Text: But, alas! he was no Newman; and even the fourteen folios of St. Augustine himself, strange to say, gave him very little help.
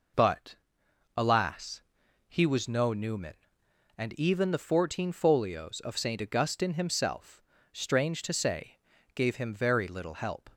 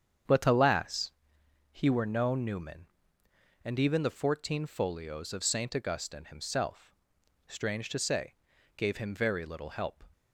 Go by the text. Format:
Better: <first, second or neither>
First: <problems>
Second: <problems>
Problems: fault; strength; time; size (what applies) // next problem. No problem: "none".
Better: first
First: none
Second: starts louder than the rest; strong; until 1.8 s; 7.5 dB // says "were" for "was"; at 1.8 s